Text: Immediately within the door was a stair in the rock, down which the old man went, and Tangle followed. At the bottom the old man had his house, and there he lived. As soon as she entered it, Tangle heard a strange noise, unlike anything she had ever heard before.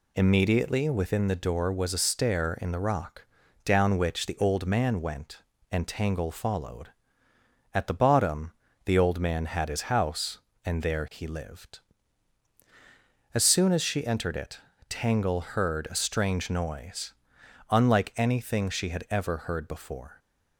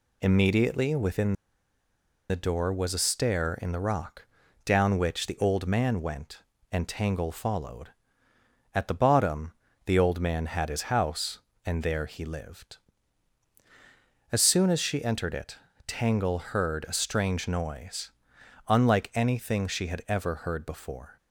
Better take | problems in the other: first | pauses between "within" and "the"; noticeable; at 1.3 s; 0.95 s long // pauses between "bottom" and "the"; slight; at 9.5 s; 0.34 s long; slight in the first

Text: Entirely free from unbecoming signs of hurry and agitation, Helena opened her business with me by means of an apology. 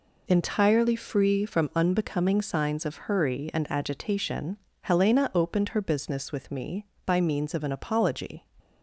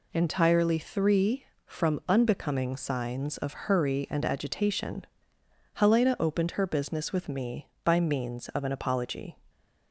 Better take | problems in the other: first | says "three" for "free"; at 0.7 s

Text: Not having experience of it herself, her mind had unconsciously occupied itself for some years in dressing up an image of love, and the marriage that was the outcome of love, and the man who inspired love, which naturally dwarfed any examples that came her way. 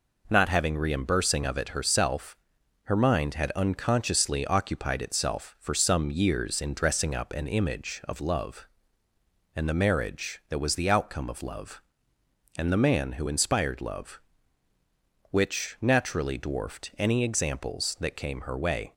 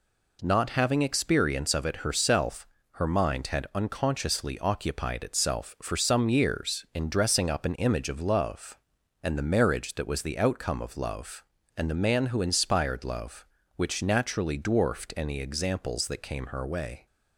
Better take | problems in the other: second | says "reimbursing" for "experience"; at 0.7 s

